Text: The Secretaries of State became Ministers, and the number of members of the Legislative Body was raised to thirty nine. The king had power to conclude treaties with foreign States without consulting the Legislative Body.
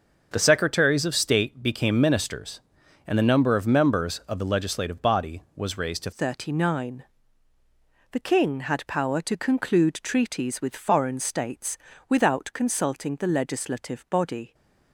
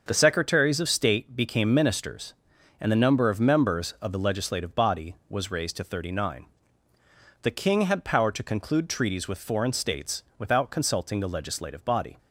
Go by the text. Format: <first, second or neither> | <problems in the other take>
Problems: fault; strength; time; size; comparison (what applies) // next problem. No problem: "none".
second | starts louder than the rest; until 1.3 s; 6 dB; also in the second // changes voice at "thirty"; from 6.1 s on; 8.4 s long // pauses between "States" and "without"; slight; at 11.7 s; 0.32 s long; slight in the second